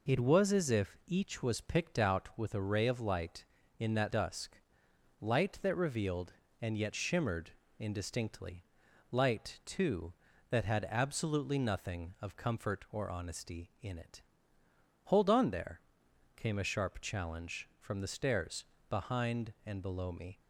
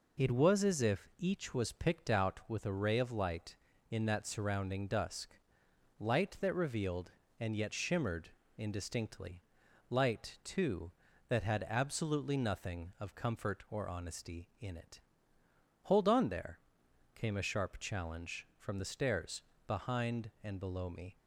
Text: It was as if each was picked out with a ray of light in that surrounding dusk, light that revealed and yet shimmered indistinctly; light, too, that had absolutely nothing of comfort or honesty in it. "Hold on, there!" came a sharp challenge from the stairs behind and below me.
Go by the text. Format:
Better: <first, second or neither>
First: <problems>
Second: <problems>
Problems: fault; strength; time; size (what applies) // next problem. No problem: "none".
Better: second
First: skips "surrounding"; at 4.1 s // pauses between "shimmered" and "indistinctly"; slight; at 7.5 s; 0.26 s long // pauses between "stairs" and "behind"; slight; at 18.6 s; 0.24 s long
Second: pauses between "shimmered" and "indistinctly"; slight; at 8.3 s; 0.26 s long // pauses between "stairs" and "behind"; slight; at 19.4 s; 0.24 s long